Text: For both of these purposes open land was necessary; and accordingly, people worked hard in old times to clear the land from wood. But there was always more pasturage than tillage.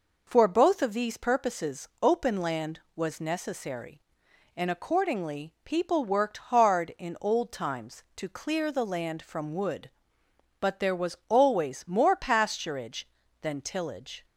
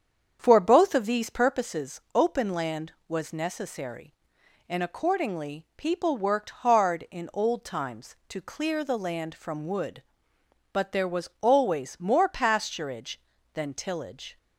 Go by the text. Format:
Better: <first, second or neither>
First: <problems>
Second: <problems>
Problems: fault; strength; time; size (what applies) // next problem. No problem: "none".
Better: first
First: pauses between "purposes" and "open"; slight; at 1.8 s; 0.16 s long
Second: starts louder than the rest; strong; until 1.7 s; 7.5 dB // pauses between "purposes" and "open"; slight; at 1.9 s; 0.16 s long